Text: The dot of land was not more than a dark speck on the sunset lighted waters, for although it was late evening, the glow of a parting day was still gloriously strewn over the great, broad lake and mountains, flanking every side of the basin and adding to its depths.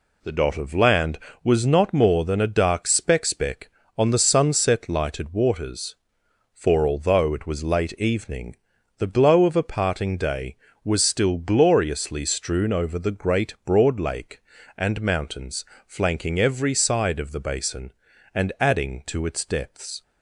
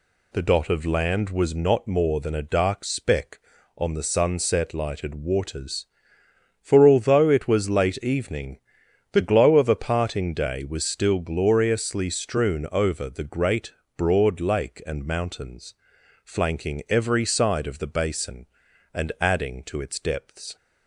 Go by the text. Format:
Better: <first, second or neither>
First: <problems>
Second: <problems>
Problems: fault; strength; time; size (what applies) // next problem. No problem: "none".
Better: second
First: says "speck" twice; at 3.2 s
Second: none